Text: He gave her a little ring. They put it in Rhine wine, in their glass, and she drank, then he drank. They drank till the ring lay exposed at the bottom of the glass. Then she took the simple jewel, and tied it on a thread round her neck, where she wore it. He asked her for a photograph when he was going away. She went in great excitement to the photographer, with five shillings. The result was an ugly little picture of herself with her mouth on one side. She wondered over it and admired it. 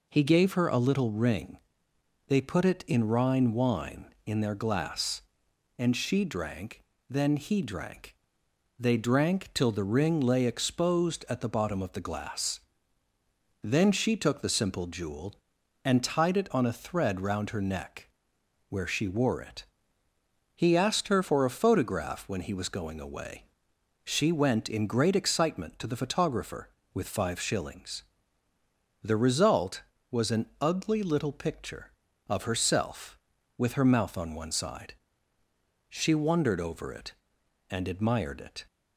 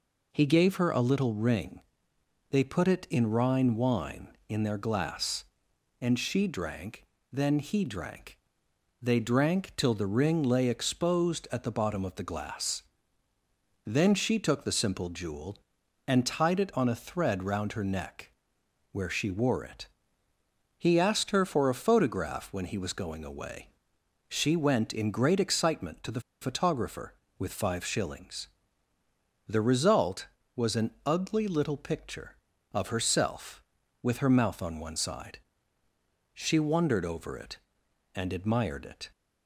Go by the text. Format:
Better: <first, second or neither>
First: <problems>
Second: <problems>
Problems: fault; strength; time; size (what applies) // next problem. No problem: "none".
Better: first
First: none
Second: pauses between "the" and "photographer"; slight; at 26.1 s; 0.21 s long